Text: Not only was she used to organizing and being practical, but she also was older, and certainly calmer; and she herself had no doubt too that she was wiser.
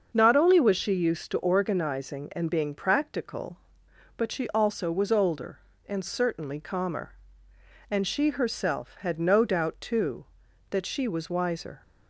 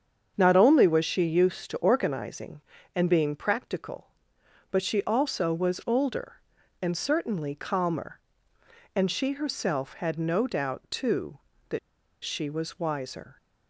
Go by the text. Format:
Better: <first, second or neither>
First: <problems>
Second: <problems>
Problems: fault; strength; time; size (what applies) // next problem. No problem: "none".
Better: first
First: starts louder than the rest; until 1.1 s; 6.5 dB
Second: starts louder than the rest; strong; until 1.3 s; 7.5 dB // pauses between "that" and "she"; at 11.7 s; 0.45 s long